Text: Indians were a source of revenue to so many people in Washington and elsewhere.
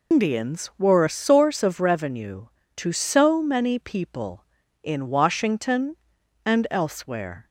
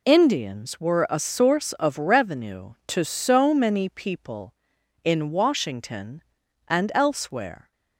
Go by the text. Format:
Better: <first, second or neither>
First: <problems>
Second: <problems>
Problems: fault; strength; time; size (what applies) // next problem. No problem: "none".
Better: second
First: loses the start of "Indians"; at 0.1 s; 160 ms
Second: none